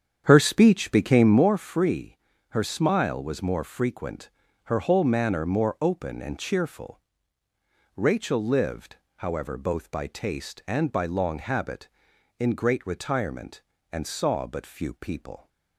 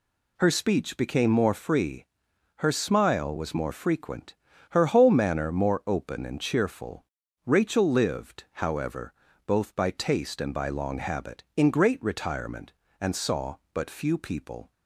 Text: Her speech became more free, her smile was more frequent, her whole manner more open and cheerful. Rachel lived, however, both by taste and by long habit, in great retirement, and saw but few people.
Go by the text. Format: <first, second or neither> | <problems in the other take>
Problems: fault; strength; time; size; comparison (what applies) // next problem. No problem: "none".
second | starts louder than the rest; strong; until 1.6 s; 8.5 dB